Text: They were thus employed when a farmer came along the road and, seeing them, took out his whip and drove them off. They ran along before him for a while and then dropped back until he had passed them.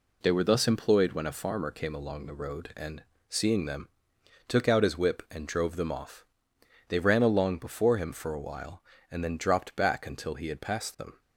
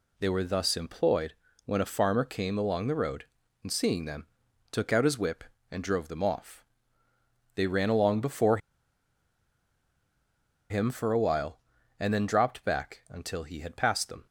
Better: first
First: none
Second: pauses between "employed" and "when"; slight; at 1.3 s; 0.30 s long // pauses between "before" and "him"; strong; at 8.5 s; 2.1 s long

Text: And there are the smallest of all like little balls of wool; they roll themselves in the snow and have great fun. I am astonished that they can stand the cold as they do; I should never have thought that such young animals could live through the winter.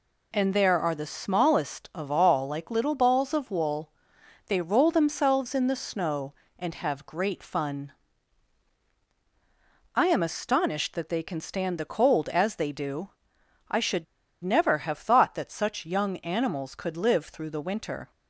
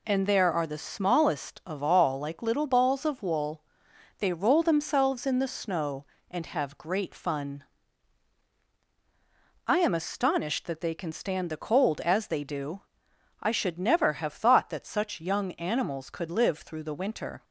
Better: second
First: pauses between "should" and "never"; at 14.0 s; 0.39 s long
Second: none

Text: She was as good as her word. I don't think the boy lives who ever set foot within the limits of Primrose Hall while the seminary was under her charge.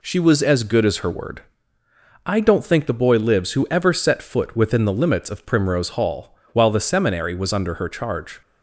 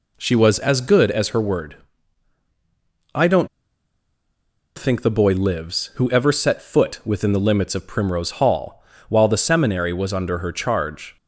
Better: first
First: pauses between "Hall" and "while"; slight; at 6.3 s; 0.18 s long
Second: pauses between "don't" and "think"; strong; at 3.4 s; 1.3 s long // pauses between "Hall" and "while"; slight; at 8.8 s; 0.26 s long

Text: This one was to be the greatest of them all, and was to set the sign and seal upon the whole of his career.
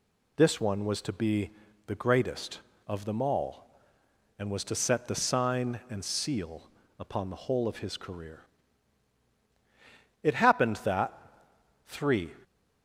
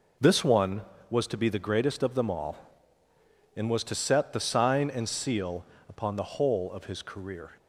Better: second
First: pauses between "be" and "the"; slight; at 1.5 s; 0.36 s long // pauses between "seal" and "upon"; slight; at 6.6 s; 0.30 s long // goes on to say "It happened that three"; strong; from 10.2 s on; 2.1 s long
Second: pauses between "seal" and "upon"; slight; at 5.6 s; 0.24 s long

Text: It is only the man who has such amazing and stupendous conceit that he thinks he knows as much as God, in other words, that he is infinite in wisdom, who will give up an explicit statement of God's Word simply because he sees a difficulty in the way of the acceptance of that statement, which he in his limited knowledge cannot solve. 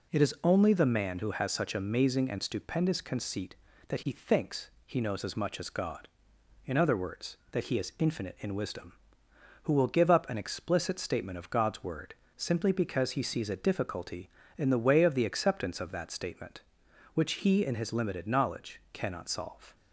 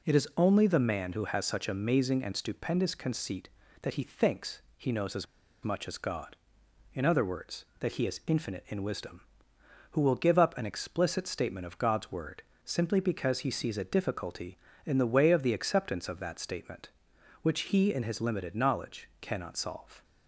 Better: first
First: pauses between "thinks" and "he"; slight; at 4.6 s; 0.16 s long // pauses between "Word" and "simply"; slight; at 12.1 s; 0.22 s long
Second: pauses between "thinks" and "he"; slight; at 4.6 s; 0.16 s long // pauses between "as" and "much"; at 5.2 s; 0.39 s long // pauses between "Word" and "simply"; slight; at 12.4 s; 0.22 s long

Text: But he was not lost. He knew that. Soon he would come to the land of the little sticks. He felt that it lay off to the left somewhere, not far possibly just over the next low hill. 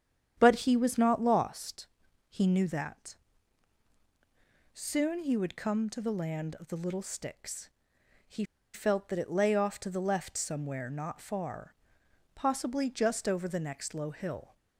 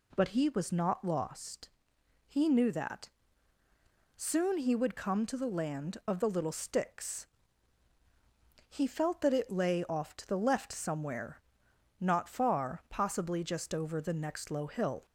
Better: second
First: starts louder than the rest; strong; until 1.3 s; 9 dB // pauses between "He" and "felt"; slight; at 8.4 s; 0.29 s long // pauses between "far" and "possibly"; noticeable; at 11.7 s; 0.62 s long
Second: none

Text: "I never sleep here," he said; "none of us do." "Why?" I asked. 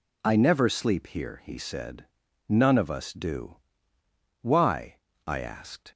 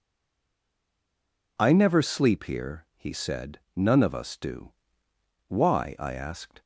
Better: first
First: none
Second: stays silent before the first word; noticeable; until 1.5 s; 1.5 s long

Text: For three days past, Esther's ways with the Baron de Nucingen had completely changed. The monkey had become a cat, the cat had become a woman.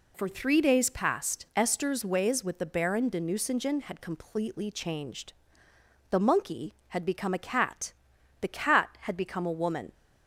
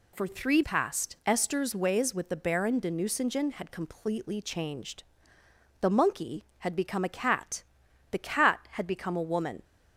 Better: first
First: none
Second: skips "days"; at 0.6 s

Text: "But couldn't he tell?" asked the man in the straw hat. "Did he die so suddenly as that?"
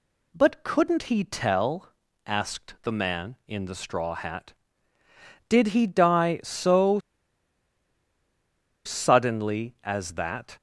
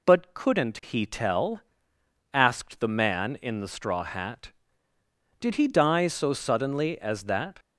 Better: second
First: pauses between "so" and "suddenly"; strong; at 6.9 s; 1.8 s long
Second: none

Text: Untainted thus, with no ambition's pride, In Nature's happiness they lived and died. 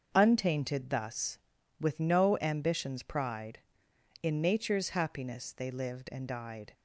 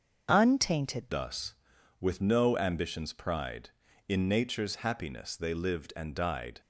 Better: first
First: starts louder than the rest; until 1.1 s; 6.5 dB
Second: starts louder than the rest; until 1.3 s; 6.5 dB // changes voice at "thus"; from 1.0 s on; 5.6 s long

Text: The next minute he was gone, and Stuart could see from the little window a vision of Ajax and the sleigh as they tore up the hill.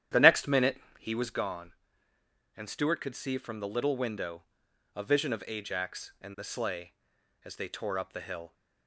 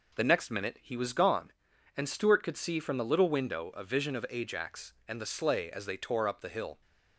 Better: second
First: starts louder than the rest; strong; until 1.2 s; 10.5 dB // pauses between "minute" and "he"; slight; at 0.7 s; 0.22 s long // pauses between "window" and "a"; noticeable; at 4.4 s; 0.52 s long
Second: none

